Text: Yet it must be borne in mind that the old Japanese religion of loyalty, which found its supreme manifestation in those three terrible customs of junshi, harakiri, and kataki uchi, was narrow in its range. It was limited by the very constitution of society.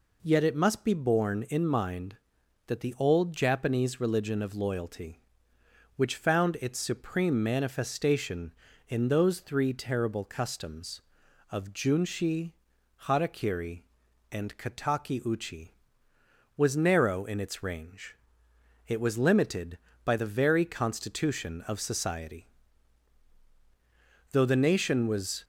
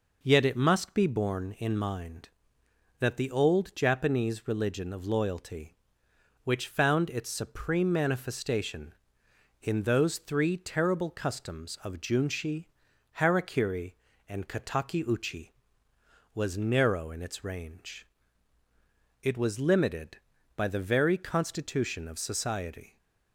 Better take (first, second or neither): second